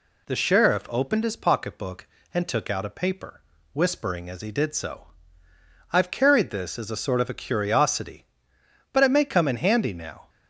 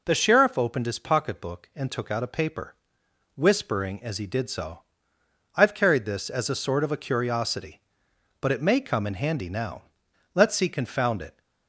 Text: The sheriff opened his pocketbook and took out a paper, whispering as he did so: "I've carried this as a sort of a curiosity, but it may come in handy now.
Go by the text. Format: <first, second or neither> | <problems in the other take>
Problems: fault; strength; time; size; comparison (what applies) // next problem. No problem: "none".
first | goes on to say "Let's see confound it"; noticeable; from 10.3 s on; 1.0 s long